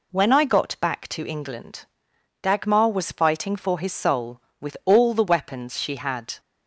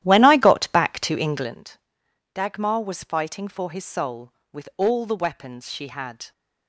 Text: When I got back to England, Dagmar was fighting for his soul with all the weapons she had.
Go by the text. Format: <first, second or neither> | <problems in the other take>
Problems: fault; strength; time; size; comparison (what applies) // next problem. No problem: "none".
first | starts louder than the rest; strong; until 1.6 s; 13 dB